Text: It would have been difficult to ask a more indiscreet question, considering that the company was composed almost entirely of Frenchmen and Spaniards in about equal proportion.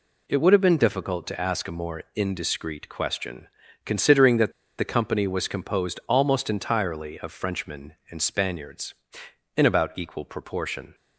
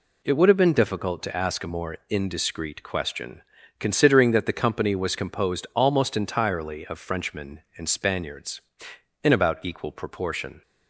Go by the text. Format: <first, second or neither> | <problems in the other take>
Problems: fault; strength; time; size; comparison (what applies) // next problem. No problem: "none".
second | pauses between "that" and "the"; slight; at 4.5 s; 0.28 s long